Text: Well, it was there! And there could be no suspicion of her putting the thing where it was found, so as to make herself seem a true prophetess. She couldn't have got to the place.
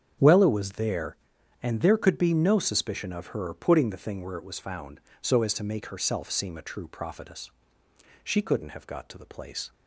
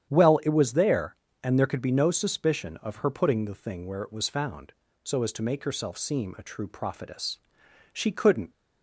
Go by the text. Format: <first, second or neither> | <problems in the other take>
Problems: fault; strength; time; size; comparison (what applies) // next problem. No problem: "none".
first | starts louder than the rest; strong; until 1.1 s; 9.5 dB; strong in the first // stops before "have got to the place"; at 8.5 s